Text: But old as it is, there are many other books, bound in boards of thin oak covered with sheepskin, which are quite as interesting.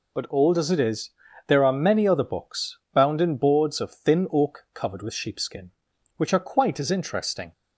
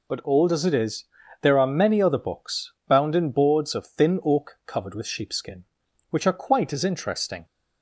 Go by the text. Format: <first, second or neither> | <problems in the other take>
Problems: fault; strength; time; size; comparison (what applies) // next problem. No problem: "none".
neither | none